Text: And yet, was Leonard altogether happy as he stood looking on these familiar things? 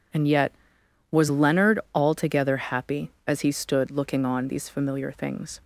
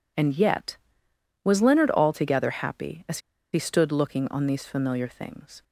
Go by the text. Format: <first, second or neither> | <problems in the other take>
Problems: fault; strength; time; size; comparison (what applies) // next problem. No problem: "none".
first | pauses between "as" and "he"; slight; at 3.1 s; 0.34 s long